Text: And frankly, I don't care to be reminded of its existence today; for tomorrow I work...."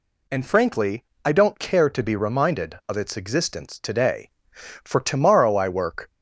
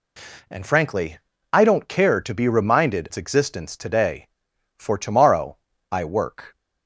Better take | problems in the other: first | skips "of"; at 3.0 s // pauses between "tomorrow" and "I"; slight; at 5.5 s; 0.34 s long

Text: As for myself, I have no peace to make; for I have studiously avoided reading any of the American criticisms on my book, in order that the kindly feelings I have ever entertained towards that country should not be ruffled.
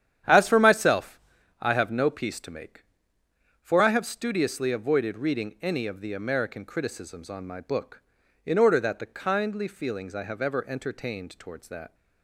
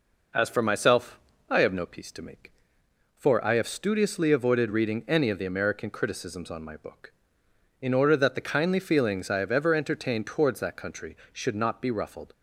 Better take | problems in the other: second | starts louder than the rest; strong; until 1.6 s; 10 dB // stops before "country should not be ruffled"; at 11.9 s

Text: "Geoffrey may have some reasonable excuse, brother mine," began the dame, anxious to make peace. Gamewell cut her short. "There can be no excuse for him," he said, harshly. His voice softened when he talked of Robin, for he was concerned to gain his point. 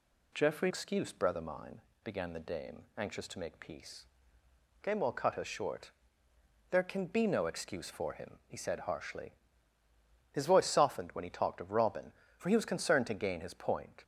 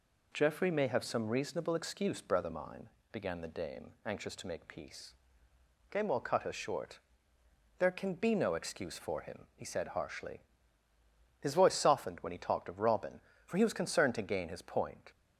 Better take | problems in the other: second | skips "may have some reasonable"; at 0.7 s

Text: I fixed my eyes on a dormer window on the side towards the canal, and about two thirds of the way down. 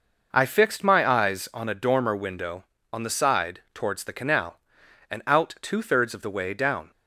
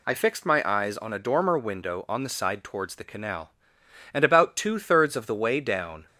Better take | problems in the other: second | says "out" for "about"; at 5.2 s

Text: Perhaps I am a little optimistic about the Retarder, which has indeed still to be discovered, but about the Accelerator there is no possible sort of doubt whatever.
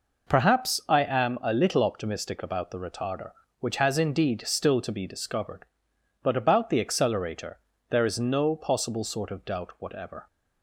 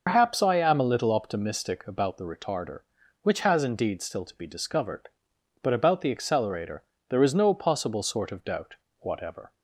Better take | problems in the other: first | loses the start of "Perhaps"; at 0.0 s; 95 ms // pauses between "Accelerator" and "there"; slight; at 6.8 s; 0.28 s long; slight in the first // pauses between "doubt" and "whatever"; slight; at 8.7 s; 0.24 s long

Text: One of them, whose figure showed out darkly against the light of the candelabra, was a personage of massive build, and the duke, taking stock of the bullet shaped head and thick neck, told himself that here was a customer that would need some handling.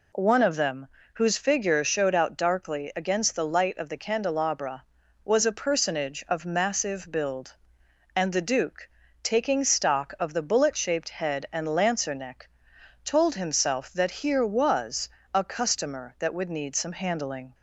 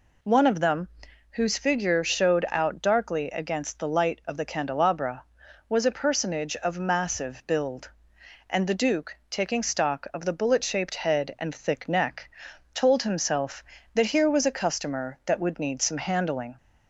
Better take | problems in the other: second | says "lancer" for "thick"; at 11.6 s // pauses between "was" and "a"; slight; at 15.0 s; 0.24 s long

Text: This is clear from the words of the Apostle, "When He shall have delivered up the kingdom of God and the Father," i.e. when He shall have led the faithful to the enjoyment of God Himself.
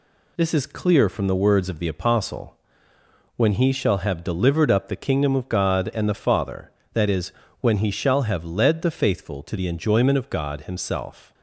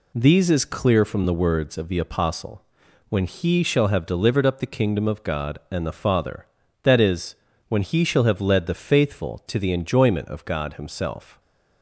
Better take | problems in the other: first | says "These" for "This"; at 0.1 s

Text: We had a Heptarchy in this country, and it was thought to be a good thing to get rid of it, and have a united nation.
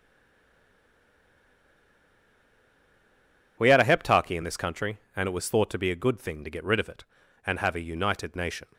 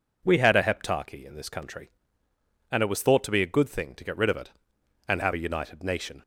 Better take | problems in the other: second | stays silent before the first word; strong; until 3.5 s; 3.5 s long

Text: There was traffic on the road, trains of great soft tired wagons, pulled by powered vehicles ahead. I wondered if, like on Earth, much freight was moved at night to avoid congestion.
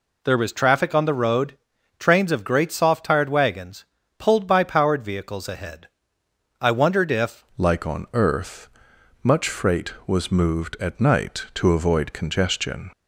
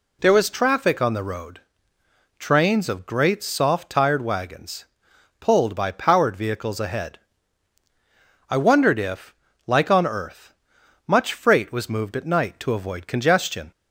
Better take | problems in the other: second | changes voice at "like"; from 7.5 s on; 5.3 s long

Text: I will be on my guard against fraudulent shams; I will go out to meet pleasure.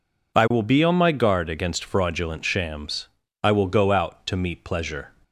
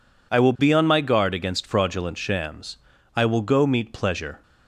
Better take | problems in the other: first | skips "out to"; at 3.6 s

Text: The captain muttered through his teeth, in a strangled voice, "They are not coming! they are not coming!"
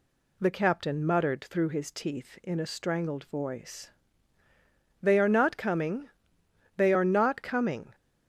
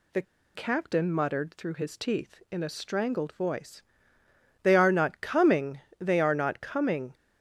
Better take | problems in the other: first | pauses between "The" and "captain"; slight; at 0.2 s; 0.32 s long

